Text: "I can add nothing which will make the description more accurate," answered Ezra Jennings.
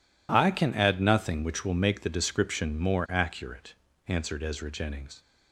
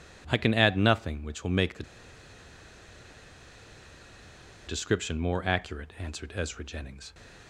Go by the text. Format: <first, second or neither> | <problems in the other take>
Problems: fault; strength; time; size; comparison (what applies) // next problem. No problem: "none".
first | pauses between "the" and "description"; strong; at 1.8 s; 2.8 s long // stays silent after the last word; slight; from 6.9 s on; 0.5 s long